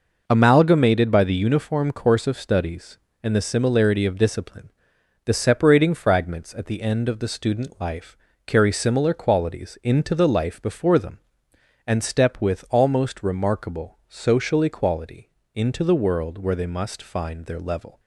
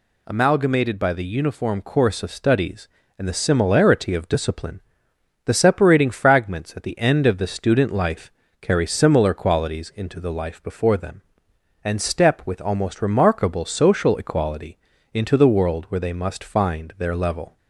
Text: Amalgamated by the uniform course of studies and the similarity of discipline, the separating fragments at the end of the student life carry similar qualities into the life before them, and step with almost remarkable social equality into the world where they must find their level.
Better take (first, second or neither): neither